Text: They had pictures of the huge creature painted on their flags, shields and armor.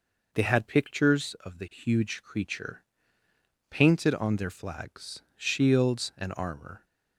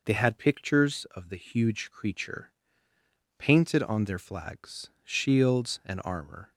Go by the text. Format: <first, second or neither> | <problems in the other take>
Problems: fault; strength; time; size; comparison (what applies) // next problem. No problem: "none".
neither | pauses between "creature" and "painted"; noticeable; the same in both